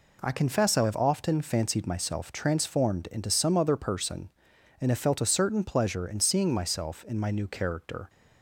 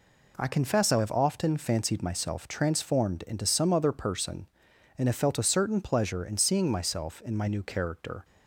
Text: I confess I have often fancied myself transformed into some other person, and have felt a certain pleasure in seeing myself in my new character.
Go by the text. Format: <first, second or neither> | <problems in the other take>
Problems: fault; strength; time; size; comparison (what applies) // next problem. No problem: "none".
neither | none